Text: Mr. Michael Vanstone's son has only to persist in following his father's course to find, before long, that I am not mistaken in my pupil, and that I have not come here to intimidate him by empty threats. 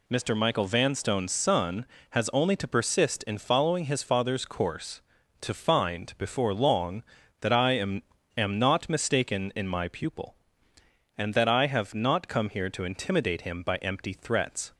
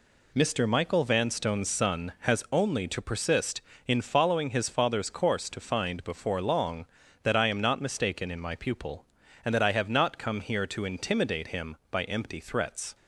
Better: second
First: says "am" twice; at 8.3 s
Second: none

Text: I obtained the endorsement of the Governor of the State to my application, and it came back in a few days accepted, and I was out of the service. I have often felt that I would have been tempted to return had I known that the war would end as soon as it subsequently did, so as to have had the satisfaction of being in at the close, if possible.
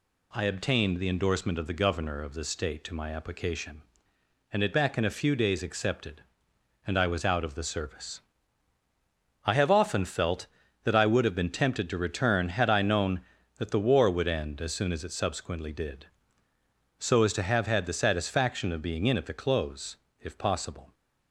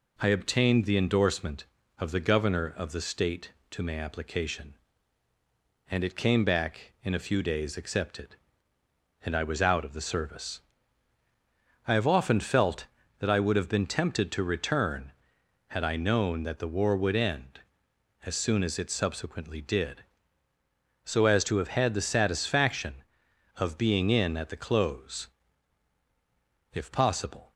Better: second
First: skips "came"; at 4.7 s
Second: none

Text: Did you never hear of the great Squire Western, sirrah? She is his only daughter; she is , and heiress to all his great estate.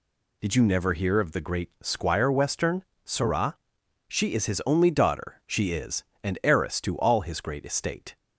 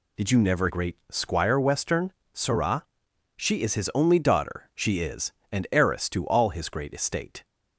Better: first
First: none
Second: skips "hear of the"; at 0.6 s

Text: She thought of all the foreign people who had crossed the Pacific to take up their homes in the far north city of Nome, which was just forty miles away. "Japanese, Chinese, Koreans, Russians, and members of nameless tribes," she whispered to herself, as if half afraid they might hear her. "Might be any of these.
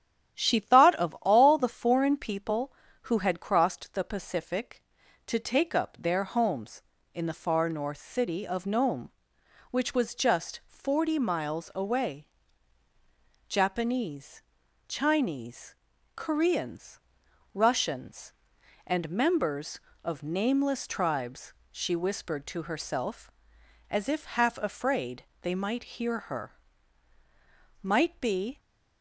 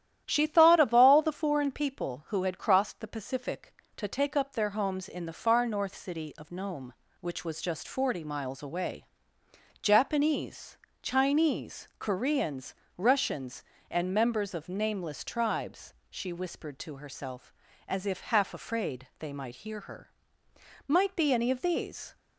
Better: second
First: starts louder than the rest; strong; until 1.4 s; 11 dB // pauses between "afraid" and "they"; slight; at 25.2 s; 0.20 s long // stops before "any of these"; at 28.5 s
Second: starts louder than the rest; strong; until 1.2 s; 11.5 dB

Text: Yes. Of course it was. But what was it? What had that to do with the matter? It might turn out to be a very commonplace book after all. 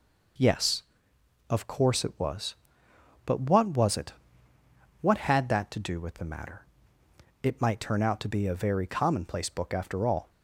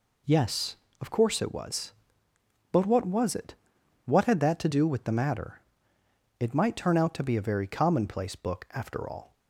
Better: neither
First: none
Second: none

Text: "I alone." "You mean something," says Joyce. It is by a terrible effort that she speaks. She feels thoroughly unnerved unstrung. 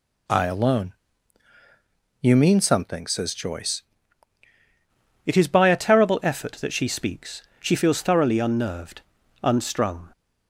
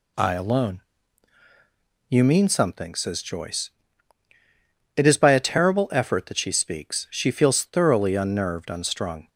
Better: second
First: changes voice at "It"; from 5.2 s on; 4.9 s long // pauses between "unnerved" and "unstrung"; at 9.0 s; 0.40 s long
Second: none

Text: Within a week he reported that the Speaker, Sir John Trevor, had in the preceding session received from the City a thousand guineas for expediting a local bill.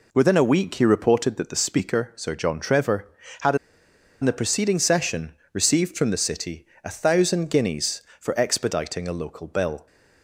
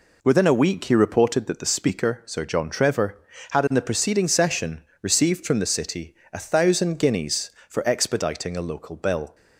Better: second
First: pauses between "in" and "the"; noticeable; at 3.5 s; 0.66 s long // pauses between "session" and "received"; slight; at 5.3 s; 0.16 s long // pauses between "City" and "a"; slight; at 6.6 s; 0.18 s long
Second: pauses between "session" and "received"; slight; at 4.8 s; 0.16 s long // pauses between "City" and "a"; slight; at 6.1 s; 0.18 s long

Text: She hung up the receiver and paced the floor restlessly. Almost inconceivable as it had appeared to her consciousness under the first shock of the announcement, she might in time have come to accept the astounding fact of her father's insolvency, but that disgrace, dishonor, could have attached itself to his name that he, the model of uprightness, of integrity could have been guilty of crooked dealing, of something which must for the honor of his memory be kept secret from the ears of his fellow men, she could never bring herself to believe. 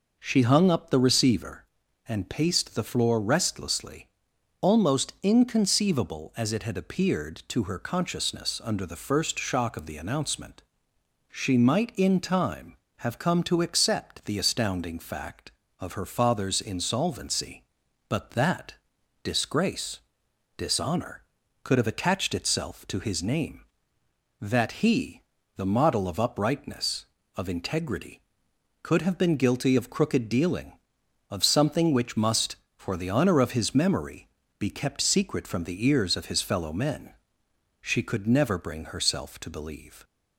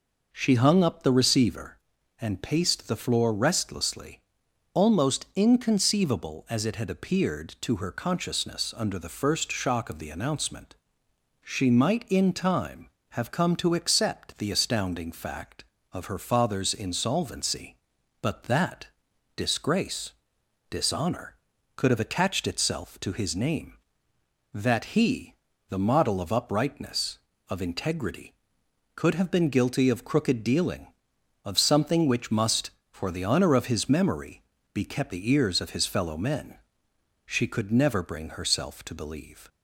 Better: first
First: pauses between "that" and "disgrace"; noticeable; at 18.7 s; 0.50 s long // pauses between "memory" and "be"; slight; at 34.2 s; 0.34 s long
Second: pauses between "that" and "disgrace"; noticeable; at 18.8 s; 0.50 s long // pauses between "memory" and "be"; slight; at 34.4 s; 0.34 s long // skips "secret from"; at 35.1 s

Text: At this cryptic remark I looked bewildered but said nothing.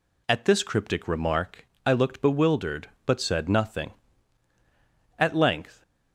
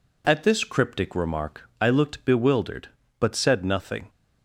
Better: second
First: pauses between "remark" and "I"; slight; at 1.6 s; 0.18 s long // goes on to say "At length"; noticeable; from 5.1 s on; 0.64 s long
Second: none

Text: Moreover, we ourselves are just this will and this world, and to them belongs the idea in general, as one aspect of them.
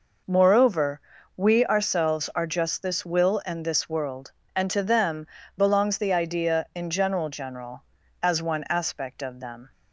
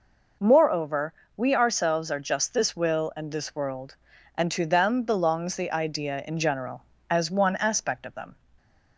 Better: second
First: pauses between "them" and "belongs"; slight; at 5.2 s; 0.32 s long // says "general" twice; at 7.2 s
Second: none

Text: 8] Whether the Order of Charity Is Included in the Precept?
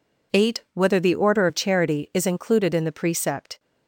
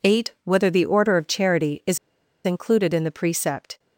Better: first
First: none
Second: pauses between "Is" and "Included"; noticeable; at 1.9 s; 0.46 s long

